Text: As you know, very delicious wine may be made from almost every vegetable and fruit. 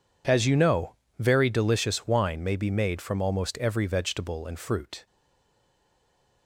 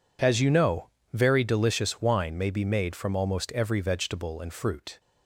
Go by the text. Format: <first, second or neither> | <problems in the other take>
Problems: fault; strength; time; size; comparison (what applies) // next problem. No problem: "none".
second | stays silent after the last word; noticeable; from 5.0 s on; 1.4 s long